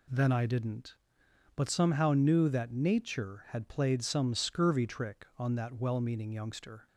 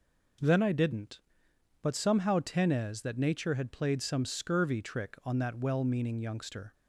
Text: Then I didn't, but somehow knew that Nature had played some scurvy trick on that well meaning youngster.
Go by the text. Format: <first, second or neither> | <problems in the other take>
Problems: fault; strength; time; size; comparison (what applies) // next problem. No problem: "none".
first | says "tenez" for "knew"; at 2.3 s